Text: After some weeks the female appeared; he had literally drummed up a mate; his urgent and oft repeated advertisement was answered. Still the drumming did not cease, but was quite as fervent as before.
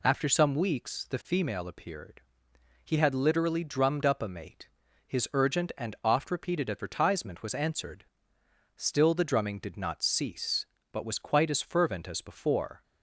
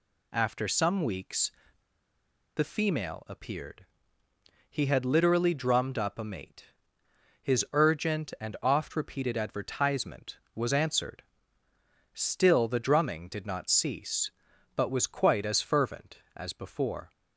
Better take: first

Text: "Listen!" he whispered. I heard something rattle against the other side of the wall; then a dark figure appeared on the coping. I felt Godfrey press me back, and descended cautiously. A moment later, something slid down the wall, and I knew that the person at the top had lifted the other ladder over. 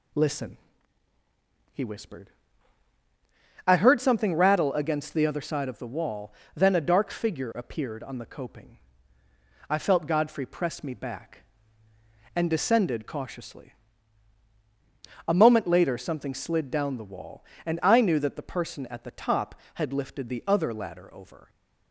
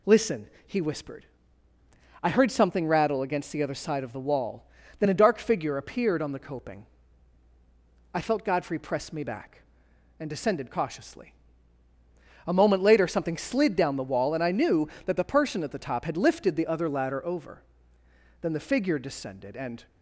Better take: first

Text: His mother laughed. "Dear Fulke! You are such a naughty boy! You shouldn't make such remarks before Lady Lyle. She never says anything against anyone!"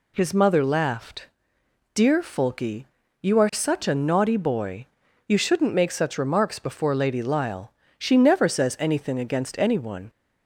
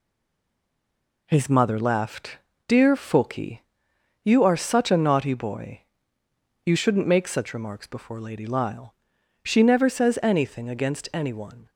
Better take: first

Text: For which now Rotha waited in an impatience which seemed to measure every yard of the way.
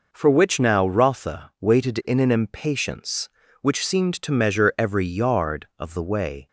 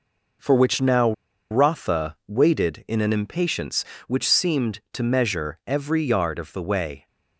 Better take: first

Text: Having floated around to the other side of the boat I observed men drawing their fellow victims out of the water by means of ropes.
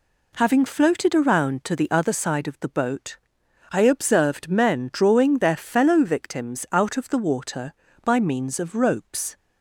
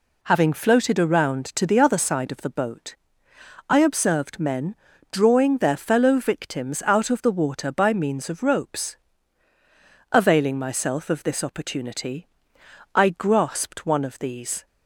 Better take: first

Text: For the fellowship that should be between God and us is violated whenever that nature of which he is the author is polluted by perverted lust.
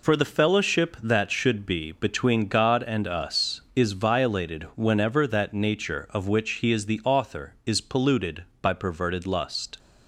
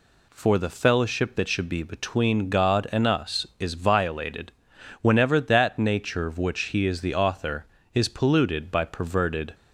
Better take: first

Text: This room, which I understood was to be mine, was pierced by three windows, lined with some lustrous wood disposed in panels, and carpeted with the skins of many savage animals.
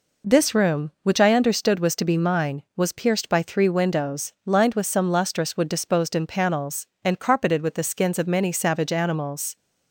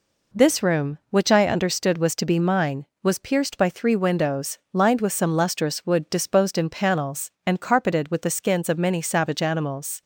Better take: neither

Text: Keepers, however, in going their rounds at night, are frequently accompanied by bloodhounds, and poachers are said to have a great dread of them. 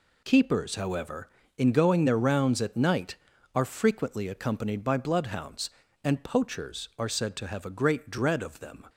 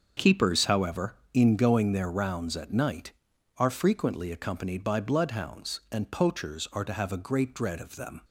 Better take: first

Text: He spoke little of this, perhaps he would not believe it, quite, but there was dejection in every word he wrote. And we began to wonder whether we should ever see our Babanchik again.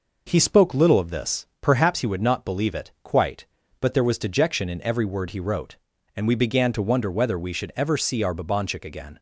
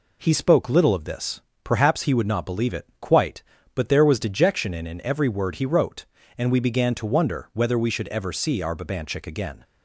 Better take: first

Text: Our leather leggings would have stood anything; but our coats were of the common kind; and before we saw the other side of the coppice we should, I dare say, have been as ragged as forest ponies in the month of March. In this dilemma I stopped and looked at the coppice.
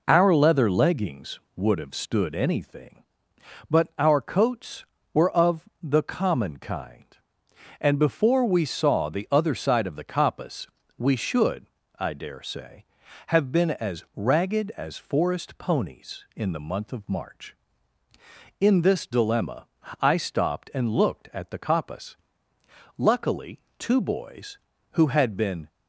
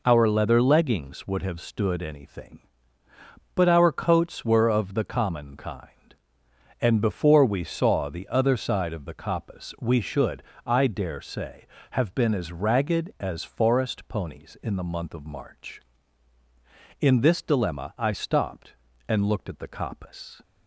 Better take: second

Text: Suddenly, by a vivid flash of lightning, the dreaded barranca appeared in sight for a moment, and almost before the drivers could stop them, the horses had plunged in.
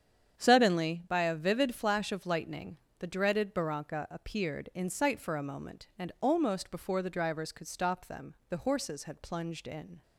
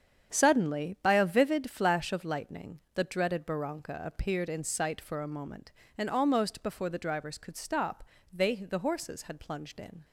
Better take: first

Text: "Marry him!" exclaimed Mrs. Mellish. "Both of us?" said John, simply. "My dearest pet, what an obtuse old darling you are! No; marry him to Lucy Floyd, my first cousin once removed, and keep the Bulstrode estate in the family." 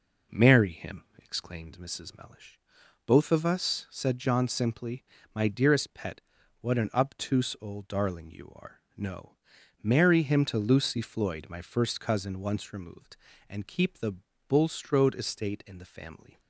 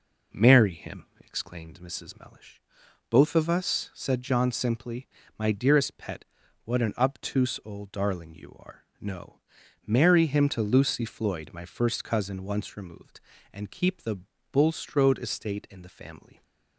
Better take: neither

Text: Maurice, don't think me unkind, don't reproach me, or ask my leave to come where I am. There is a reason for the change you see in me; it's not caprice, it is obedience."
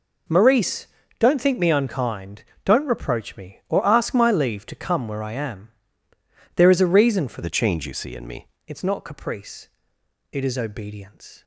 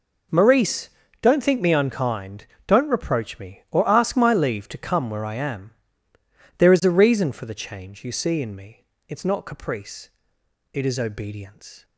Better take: second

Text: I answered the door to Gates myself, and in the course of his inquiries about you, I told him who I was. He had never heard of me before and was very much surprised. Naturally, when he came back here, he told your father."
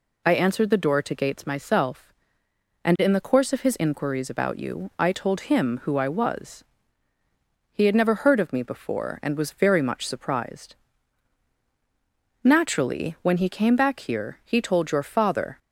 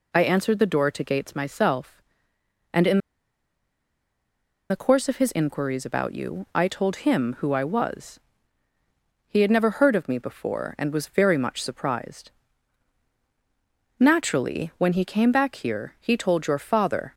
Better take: first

